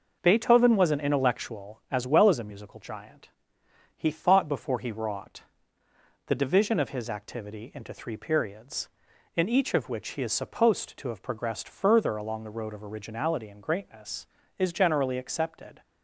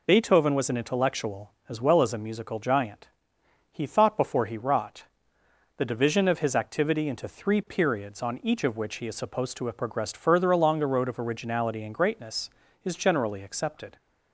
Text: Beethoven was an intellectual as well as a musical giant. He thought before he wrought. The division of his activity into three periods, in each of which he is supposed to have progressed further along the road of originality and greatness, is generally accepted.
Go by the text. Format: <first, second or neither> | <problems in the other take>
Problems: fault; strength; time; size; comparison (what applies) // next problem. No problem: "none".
first | says "on" for "in"; at 8.2 s